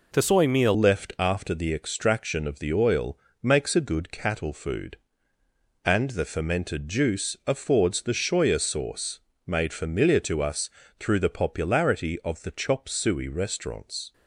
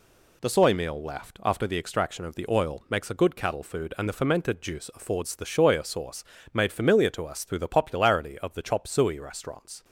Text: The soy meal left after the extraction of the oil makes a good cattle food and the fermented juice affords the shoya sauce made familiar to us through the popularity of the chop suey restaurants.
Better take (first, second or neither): second